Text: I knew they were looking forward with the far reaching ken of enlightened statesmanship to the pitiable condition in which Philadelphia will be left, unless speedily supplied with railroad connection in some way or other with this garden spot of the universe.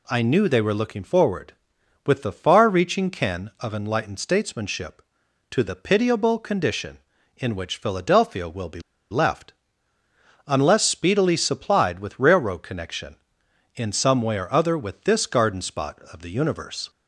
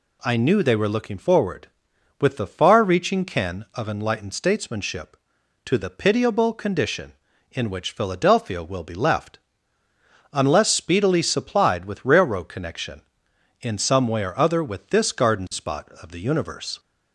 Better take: second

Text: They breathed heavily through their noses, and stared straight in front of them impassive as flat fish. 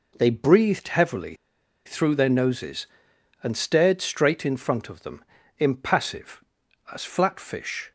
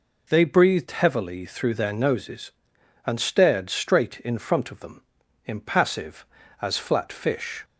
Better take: second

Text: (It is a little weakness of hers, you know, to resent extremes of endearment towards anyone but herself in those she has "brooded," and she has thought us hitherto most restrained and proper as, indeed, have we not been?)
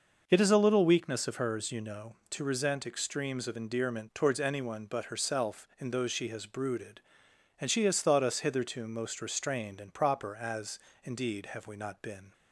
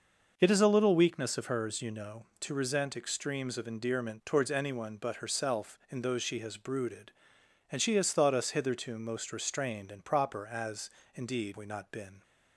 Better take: first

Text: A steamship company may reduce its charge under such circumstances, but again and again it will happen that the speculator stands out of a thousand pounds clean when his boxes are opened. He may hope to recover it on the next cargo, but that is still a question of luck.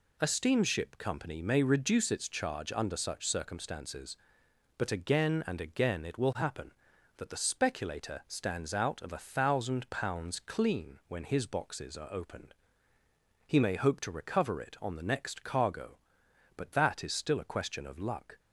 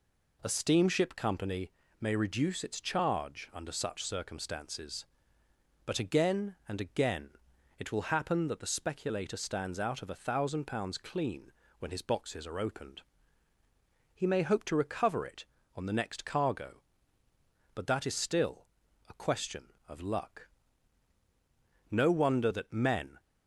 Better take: first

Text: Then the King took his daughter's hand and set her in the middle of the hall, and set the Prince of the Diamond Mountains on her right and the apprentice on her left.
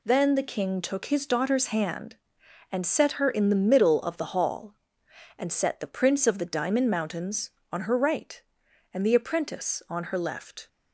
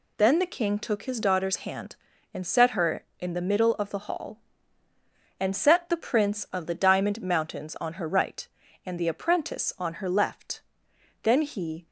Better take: first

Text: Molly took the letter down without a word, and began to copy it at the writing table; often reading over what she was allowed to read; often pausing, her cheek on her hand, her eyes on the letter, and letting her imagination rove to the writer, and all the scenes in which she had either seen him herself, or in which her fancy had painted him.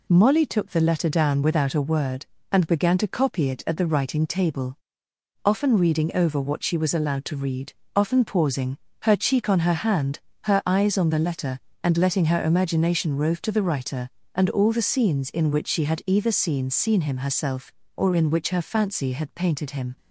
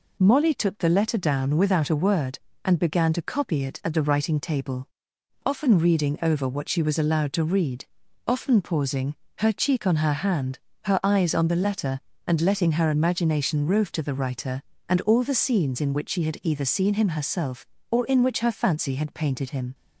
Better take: second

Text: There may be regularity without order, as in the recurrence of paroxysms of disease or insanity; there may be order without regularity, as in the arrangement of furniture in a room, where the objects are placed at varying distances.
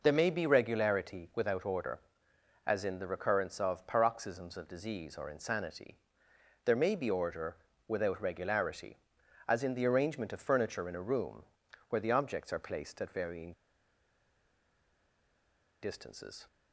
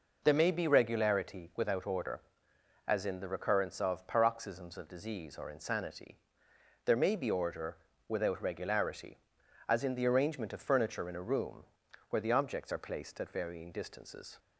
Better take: second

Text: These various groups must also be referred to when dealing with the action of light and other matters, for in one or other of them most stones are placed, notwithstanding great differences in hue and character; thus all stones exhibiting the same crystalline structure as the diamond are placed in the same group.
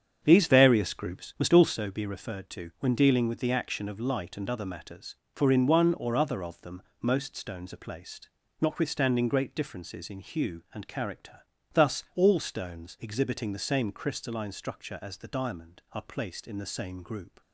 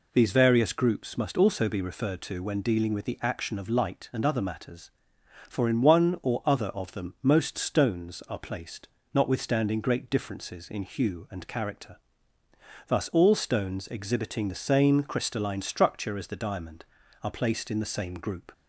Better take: second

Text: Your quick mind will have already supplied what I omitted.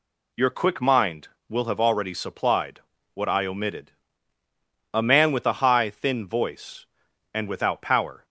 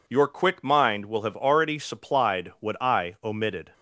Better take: second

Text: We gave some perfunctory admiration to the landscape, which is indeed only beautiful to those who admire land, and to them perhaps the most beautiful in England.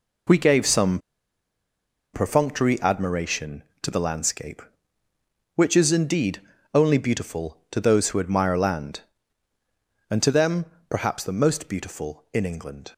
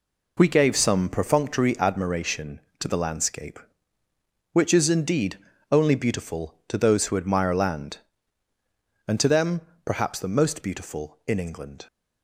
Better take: second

